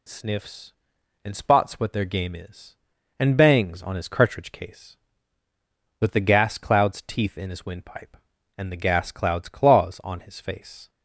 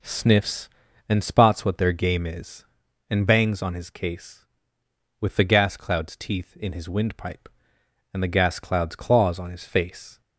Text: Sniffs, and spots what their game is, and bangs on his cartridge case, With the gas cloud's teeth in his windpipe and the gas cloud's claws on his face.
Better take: first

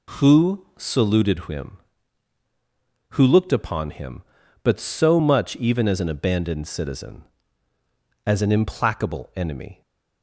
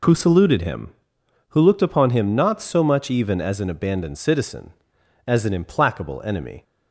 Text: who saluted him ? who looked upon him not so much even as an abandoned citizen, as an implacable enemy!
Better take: second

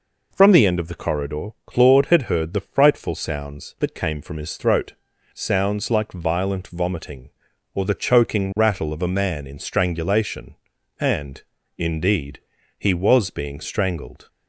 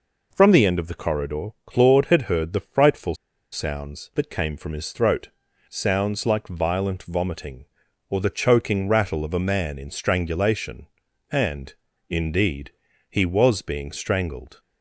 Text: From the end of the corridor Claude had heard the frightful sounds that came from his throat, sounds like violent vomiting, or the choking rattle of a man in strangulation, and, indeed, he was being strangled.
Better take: first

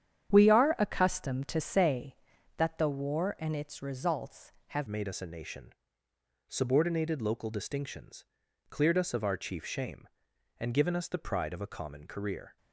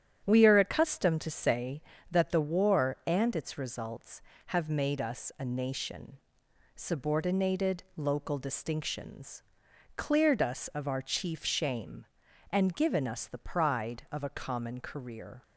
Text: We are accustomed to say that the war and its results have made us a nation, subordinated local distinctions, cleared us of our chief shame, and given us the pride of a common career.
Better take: second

